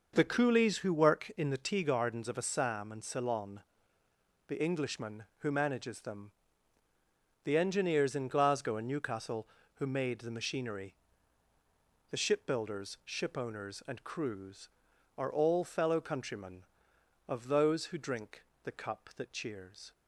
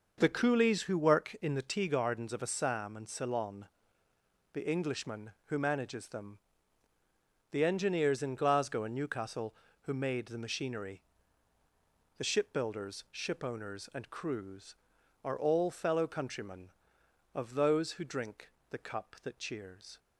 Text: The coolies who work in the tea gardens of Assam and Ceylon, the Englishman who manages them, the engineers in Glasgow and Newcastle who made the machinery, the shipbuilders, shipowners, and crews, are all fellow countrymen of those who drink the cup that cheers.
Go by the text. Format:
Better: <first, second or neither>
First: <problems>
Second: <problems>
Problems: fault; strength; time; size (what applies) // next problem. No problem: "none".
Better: neither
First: starts louder than the rest; noticeable; until 1.1 s; 6 dB // pauses between "drink" and "the"; slight; at 18.4 s; 0.22 s long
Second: starts louder than the rest; noticeable; until 1.1 s; 6 dB // pauses between "drink" and "the"; slight; at 18.4 s; 0.22 s long